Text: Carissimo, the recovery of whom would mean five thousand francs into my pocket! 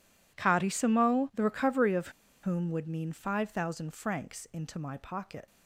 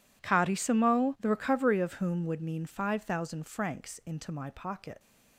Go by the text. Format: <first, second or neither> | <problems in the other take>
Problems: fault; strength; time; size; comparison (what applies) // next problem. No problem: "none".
second | pauses between "of" and "whom"; slight; at 2.0 s; 0.33 s long